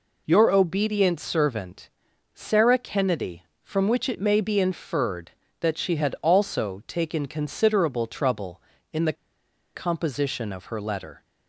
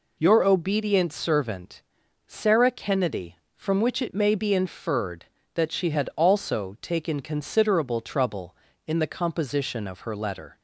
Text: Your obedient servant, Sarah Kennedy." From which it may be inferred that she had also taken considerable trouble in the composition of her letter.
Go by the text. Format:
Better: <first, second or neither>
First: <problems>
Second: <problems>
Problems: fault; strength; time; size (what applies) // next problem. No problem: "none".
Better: second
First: pauses between "the" and "composition"; noticeable; at 9.1 s; 0.62 s long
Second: none